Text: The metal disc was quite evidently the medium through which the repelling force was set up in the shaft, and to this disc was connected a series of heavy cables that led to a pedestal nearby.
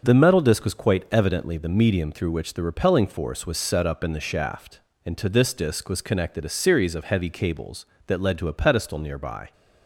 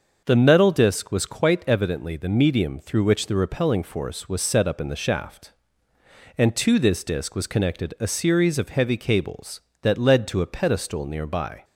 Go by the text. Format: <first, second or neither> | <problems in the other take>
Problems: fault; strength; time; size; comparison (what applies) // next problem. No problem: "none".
neither | starts louder than the rest; the same in both